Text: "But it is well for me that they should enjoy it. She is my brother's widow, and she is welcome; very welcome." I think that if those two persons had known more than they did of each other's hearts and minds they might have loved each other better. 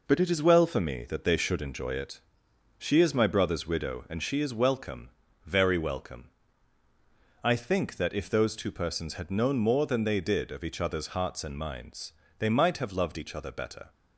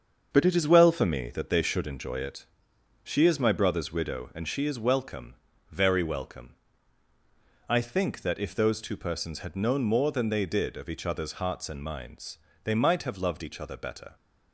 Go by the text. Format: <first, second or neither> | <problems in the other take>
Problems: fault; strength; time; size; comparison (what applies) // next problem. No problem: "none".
first | starts louder than the rest; until 1.5 s; 7 dB // pauses between "minds" and "they"; slight; at 12.3 s; 0.26 s long; slight in the first